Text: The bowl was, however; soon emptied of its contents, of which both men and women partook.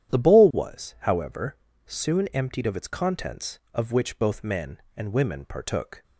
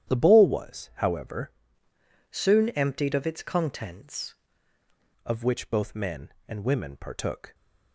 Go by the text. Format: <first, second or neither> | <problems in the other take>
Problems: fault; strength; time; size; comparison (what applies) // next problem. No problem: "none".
first | starts louder than the rest; strong; until 1.1 s; 10.5 dB; strong in the first // changes voice from "soon" to "contents"; from 2.3 to 4.3 s; 2.0 s long